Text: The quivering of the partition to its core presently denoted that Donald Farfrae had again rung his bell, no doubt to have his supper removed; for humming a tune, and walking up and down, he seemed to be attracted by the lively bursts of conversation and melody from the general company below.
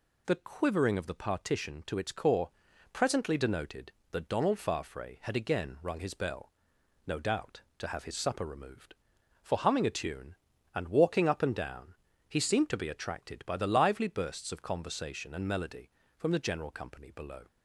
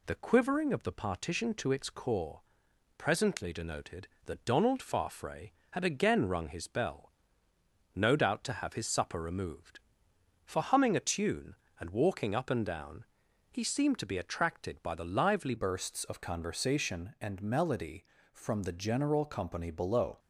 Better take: first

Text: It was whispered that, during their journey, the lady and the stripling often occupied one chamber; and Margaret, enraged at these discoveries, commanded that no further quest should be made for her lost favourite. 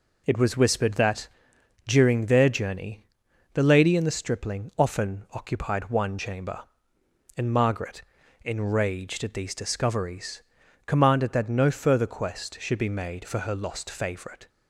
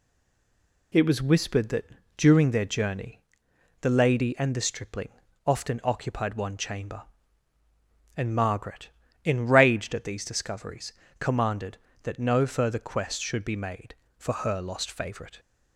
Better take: first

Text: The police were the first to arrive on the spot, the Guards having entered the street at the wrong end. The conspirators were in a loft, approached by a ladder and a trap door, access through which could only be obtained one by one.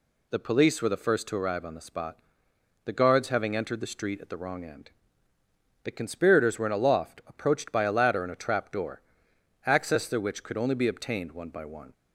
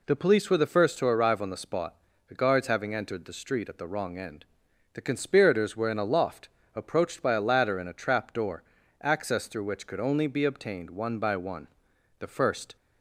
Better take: first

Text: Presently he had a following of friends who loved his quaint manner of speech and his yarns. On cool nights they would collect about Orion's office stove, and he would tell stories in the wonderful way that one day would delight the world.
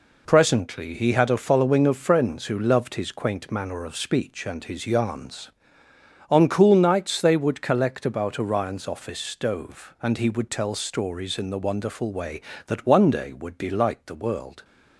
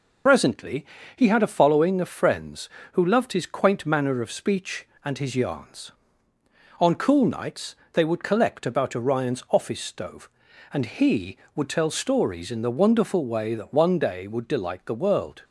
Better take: first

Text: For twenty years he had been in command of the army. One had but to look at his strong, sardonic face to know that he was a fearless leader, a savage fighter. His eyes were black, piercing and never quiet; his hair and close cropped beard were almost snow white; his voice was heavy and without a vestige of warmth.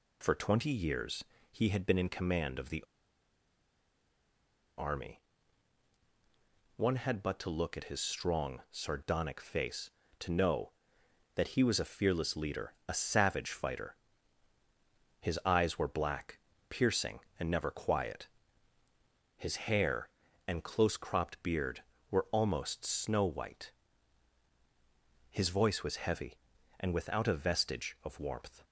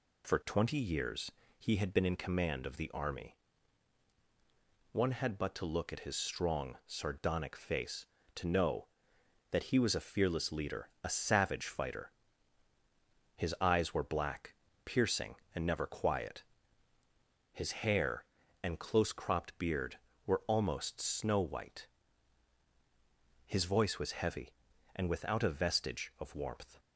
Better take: second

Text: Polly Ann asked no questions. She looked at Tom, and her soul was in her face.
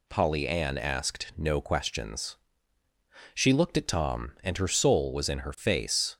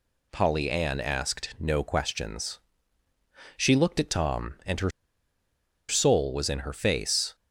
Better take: first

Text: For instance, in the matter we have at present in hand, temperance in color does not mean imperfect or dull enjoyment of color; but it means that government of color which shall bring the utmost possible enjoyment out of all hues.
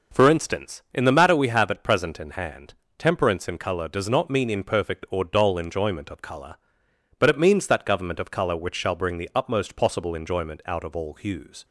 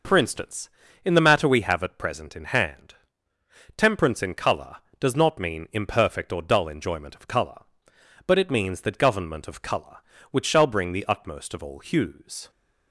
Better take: first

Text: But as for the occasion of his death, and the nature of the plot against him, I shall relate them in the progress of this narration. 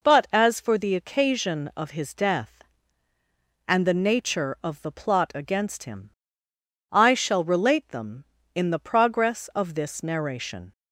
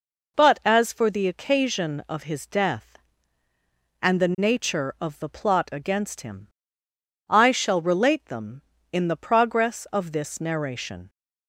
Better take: neither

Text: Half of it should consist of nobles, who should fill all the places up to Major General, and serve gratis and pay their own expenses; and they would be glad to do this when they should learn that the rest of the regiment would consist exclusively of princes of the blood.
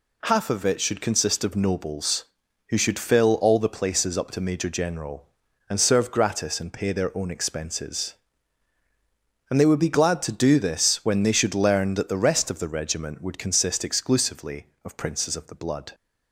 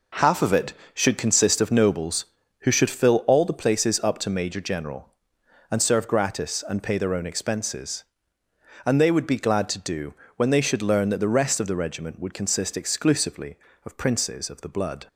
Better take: first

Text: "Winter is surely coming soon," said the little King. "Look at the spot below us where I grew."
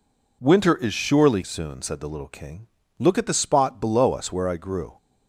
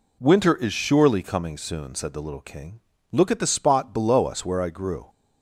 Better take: second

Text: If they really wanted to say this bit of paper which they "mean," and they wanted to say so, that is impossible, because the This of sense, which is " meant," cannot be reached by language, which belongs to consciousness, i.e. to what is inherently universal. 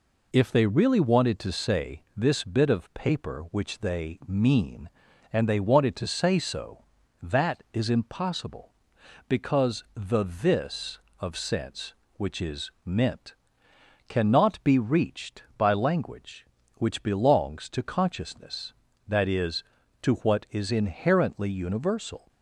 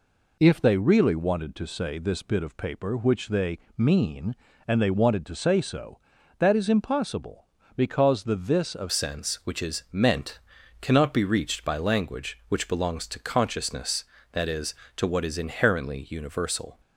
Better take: first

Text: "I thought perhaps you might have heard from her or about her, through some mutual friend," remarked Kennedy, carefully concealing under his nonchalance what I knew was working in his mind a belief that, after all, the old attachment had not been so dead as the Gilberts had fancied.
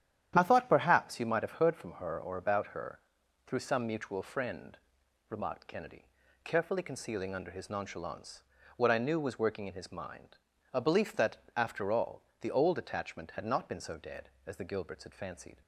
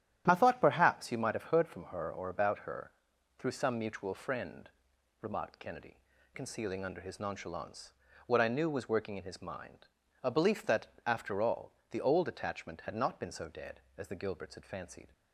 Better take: first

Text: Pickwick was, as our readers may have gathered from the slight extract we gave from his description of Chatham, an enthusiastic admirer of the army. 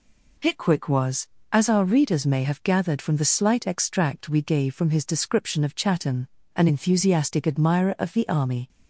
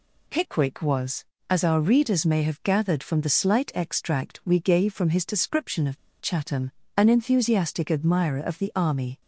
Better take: first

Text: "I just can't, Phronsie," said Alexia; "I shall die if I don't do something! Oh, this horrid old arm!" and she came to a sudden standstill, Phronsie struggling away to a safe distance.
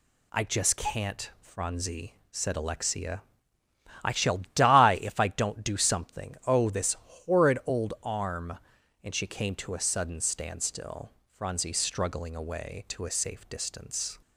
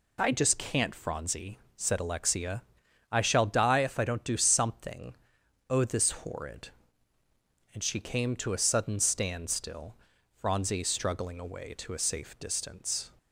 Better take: first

